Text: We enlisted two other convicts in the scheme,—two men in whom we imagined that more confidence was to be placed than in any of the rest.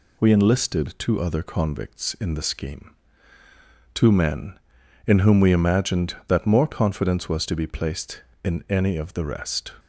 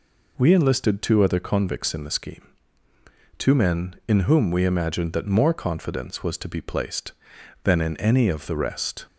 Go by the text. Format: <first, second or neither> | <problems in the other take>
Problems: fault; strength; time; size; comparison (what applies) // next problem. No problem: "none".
second | skips "than"; at 8.3 s